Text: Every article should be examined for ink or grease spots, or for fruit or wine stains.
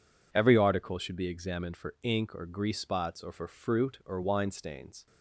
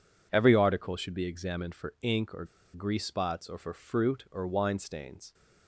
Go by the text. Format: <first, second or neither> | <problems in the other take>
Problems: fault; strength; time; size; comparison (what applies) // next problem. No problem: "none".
first | pauses between "or" and "grease"; slight; at 2.4 s; 0.28 s long